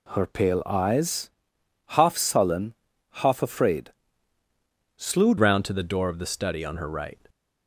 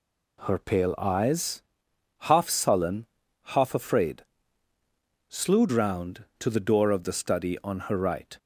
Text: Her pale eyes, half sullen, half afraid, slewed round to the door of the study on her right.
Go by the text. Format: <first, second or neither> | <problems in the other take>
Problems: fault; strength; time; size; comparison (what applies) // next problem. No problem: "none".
second | changes voice at "round"; from 5.3 s on; 1.9 s long